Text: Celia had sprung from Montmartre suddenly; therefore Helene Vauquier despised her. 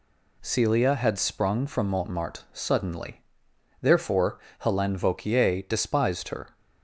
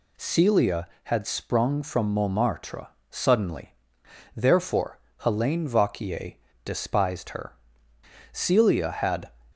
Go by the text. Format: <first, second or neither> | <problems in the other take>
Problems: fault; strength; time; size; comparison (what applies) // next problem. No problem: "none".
first | pauses between "Montmartre" and "suddenly"; slight; at 2.8 s; 0.24 s long // pauses between "therefore" and "Helene"; slight; at 4.9 s; 0.18 s long; slight in the first // pauses between "Vauquier" and "despised"; slight; at 6.3 s; 0.32 s long // goes on to say "Celia had"; noticeable; from 8.3 s on; 1.0 s long